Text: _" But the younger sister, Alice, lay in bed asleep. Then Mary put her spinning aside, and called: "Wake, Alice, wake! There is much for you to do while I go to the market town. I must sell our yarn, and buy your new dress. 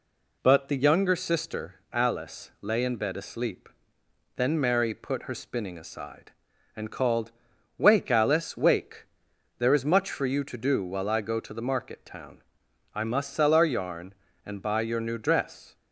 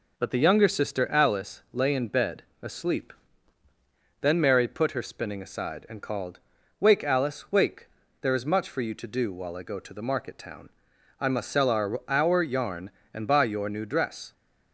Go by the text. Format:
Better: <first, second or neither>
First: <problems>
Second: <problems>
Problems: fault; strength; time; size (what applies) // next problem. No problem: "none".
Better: first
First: none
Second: pauses between "bed" and "asleep"; slight; at 2.4 s; 0.20 s long // says "our" twice; at 12.0 s